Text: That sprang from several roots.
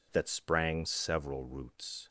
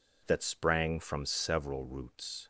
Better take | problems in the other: second | skips "from"; at 0.8 s

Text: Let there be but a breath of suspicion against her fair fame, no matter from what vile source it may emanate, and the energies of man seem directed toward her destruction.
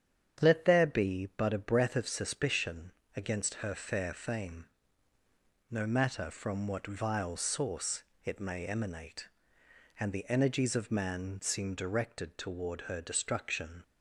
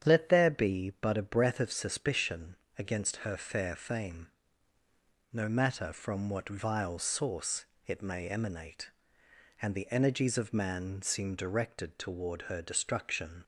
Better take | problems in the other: neither | starts louder than the rest; strong; the same in both // pauses between "suspicion" and "against"; slight; the same in both // pauses between "source" and "it"; slight; the same in both

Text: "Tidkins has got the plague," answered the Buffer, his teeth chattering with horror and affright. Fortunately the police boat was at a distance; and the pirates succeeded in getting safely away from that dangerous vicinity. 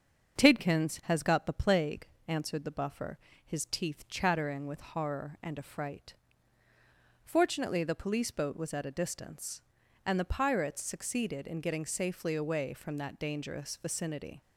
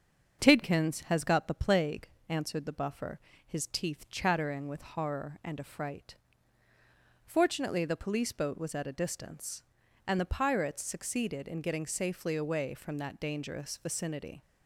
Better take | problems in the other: neither | starts louder than the rest; the same in both

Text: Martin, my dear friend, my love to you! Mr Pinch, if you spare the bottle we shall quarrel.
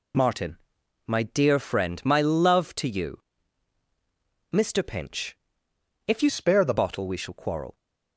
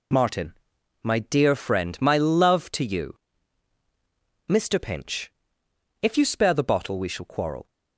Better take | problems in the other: second | changes voice from "spare" to "the"; from 6.2 to 6.7 s; 0.5 s long

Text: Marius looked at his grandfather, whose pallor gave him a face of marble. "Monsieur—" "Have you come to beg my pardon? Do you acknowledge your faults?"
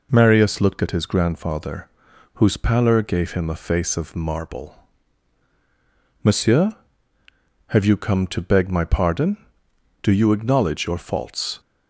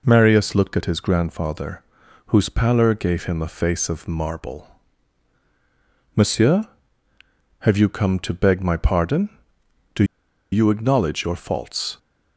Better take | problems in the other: first | pauses between "Do" and "you"; noticeable; at 10.0 s; 0.47 s long

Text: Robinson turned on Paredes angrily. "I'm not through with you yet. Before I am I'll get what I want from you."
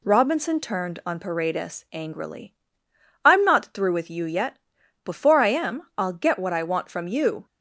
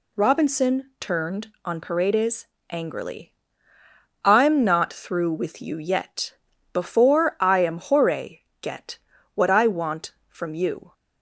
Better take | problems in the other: first | pauses between "Paredes" and "angrily"; slight; at 2.4 s; 0.24 s long // says "Hore" for "I'll"; at 7.7 s // pauses between "get" and "what"; slight; at 8.9 s; 0.34 s long

